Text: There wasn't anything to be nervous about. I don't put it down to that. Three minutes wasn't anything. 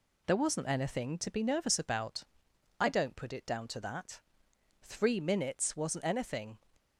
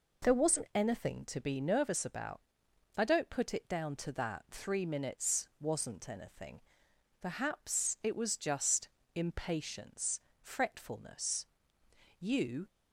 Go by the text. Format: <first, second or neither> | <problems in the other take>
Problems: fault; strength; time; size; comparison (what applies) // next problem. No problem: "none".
first | goes on to say "Perhaps it was just impatience fretfulness You"; strong; from 7.2 s on; 5.4 s long